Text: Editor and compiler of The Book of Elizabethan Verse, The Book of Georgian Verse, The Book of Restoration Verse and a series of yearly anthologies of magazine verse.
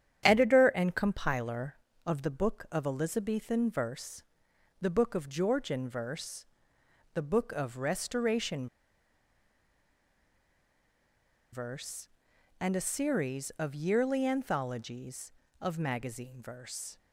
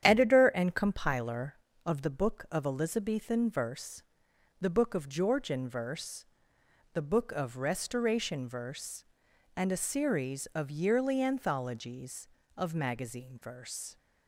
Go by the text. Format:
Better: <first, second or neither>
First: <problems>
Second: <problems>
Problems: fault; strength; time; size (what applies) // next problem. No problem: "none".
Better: second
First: starts louder than the rest; strong; until 1.2 s; 9.5 dB // pauses between "Restoration" and "Verse"; strong; at 8.6 s; 2.8 s long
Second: starts louder than the rest; strong; until 1.0 s; 9.5 dB